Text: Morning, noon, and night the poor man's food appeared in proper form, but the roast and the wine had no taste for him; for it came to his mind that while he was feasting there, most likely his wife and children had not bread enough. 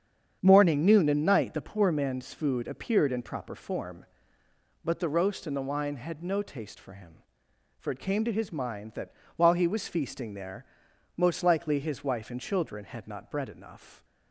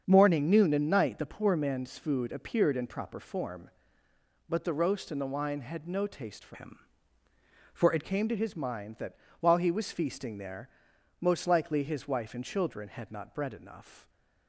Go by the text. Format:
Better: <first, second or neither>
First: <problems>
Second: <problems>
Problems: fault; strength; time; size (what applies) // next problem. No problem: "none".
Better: first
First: starts louder than the rest; strong; until 1.4 s; 8 dB // pauses between "that" and "while"; slight; at 9.1 s; 0.24 s long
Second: starts louder than the rest; strong; until 1.0 s; 7.5 dB // changes voice from "him" to "it"; from 6.5 to 8.0 s; 1.5 s long // pauses between "that" and "while"; slight; at 9.1 s; 0.24 s long